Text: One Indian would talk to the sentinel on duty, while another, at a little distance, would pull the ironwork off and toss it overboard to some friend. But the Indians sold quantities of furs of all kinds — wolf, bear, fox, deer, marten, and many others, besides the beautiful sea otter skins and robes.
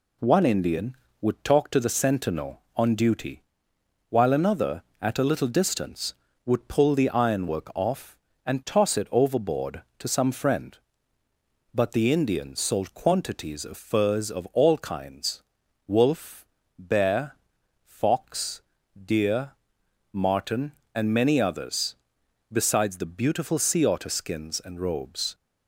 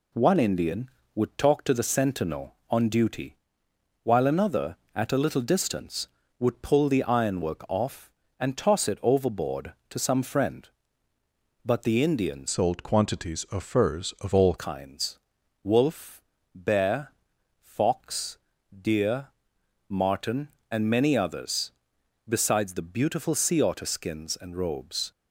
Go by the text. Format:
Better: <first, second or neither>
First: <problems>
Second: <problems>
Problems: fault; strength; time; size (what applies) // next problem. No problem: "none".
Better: first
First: none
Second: changes voice from "sold" to "all"; from 12.4 to 14.5 s; 2.1 s long